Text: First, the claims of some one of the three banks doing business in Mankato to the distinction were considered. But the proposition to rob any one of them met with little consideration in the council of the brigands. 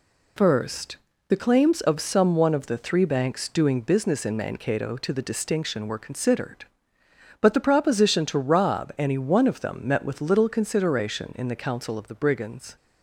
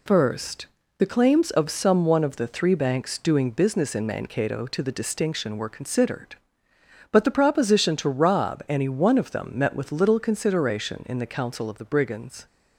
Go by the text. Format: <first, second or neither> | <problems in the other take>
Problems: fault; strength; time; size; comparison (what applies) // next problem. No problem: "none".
neither | none